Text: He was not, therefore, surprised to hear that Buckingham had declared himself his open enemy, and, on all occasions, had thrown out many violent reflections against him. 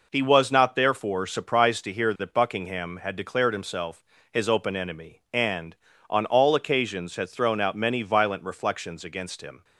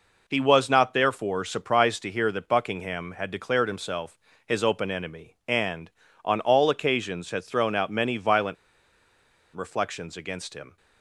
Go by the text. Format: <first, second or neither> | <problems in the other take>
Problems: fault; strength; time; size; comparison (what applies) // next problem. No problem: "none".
first | pauses between "himself" and "his"; slight; at 4.1 s; 0.26 s long; slight in the first // pauses between "violent" and "reflections"; at 8.5 s; 1.0 s long